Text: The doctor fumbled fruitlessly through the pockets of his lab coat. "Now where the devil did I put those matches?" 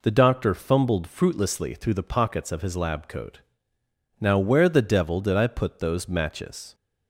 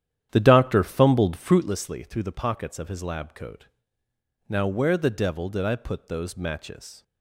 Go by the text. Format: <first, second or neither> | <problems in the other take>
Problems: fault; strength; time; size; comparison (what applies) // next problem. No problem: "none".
first | starts louder than the rest; strong; until 1.7 s; 10.5 dB